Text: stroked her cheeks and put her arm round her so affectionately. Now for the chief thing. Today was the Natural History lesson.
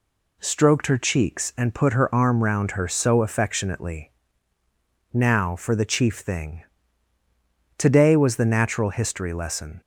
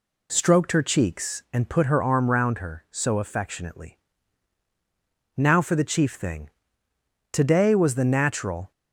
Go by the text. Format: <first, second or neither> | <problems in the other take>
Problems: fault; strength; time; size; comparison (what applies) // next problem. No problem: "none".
first | stops before "History lesson"; at 8.7 s